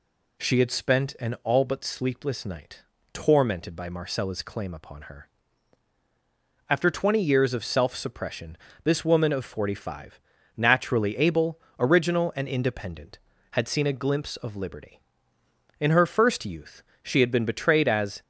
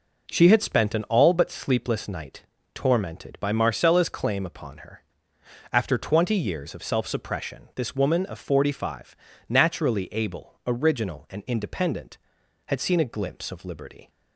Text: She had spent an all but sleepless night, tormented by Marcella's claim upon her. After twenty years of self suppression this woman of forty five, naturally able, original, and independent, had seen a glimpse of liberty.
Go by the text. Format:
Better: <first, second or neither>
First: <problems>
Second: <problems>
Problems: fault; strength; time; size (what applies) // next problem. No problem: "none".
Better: second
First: pauses between "suppression" and "this"; slight; at 8.5 s; 0.28 s long // goes on to say "In her first youth she had been betrayed as"; strong; from 15.7 s on; 2.4 s long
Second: none